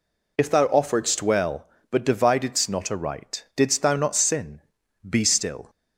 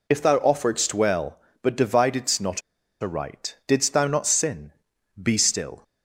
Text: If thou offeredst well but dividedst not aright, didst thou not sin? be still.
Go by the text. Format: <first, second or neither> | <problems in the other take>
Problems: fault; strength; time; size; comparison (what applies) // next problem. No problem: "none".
first | pauses between "not" and "aright"; at 2.6 s; 0.39 s long